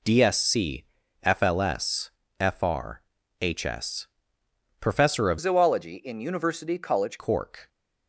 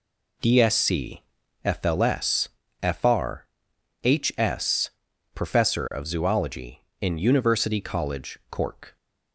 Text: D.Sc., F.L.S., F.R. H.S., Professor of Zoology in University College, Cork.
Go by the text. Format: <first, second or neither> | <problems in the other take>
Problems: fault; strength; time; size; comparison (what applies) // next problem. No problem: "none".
second | changes voice from "Zoology" to "College"; from 5.3 to 7.1 s; 1.8 s long